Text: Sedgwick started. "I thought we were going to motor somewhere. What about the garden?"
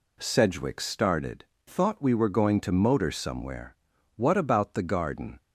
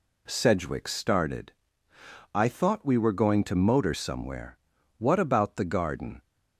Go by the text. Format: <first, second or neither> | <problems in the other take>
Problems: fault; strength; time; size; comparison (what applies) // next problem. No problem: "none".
second | skips "I"; at 1.5 s